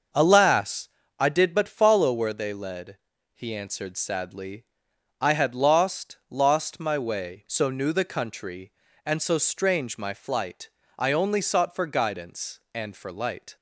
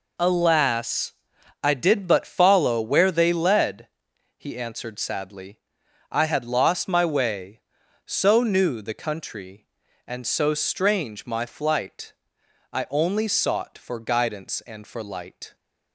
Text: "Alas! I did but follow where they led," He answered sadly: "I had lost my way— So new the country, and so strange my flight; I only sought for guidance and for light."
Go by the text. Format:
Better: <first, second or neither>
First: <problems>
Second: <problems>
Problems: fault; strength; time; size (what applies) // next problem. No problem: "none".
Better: second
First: starts louder than the rest; until 1.4 s; 6 dB // says "lost" twice; at 6.2 s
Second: none